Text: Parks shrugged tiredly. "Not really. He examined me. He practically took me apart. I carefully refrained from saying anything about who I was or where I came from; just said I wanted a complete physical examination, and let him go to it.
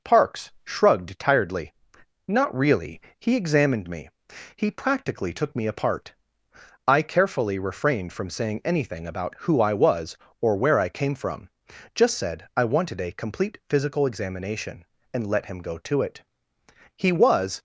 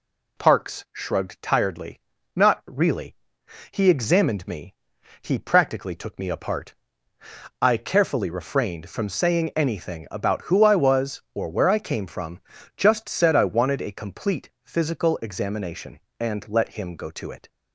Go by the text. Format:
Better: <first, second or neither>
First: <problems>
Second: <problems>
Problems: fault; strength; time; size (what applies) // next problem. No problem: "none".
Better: second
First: goes on to say "He was"; noticeable; from 16.9 s on; 0.64 s long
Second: none